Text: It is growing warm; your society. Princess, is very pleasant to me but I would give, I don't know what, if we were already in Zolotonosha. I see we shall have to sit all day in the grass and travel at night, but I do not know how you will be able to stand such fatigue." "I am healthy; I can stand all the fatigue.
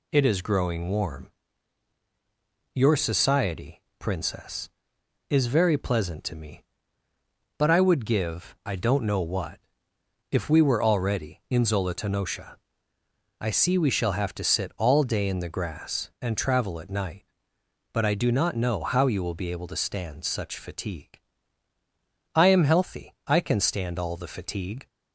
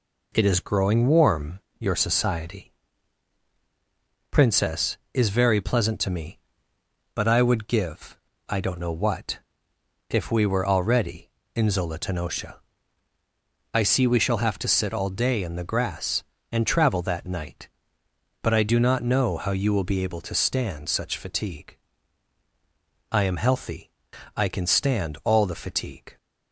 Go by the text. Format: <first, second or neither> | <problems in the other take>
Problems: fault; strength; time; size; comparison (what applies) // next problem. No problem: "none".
first | says "that" for "at"; at 17.0 s